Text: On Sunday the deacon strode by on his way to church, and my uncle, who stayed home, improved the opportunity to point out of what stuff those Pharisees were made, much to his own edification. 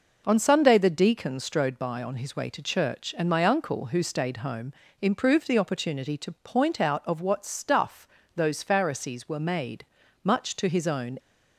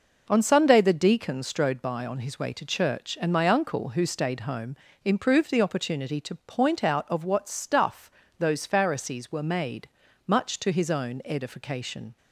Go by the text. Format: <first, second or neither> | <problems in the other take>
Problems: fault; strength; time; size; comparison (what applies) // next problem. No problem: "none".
second | pauses between "stuff" and "those"; slight; at 8.0 s; 0.26 s long; slight in the second // stops before "edification"; at 11.1 s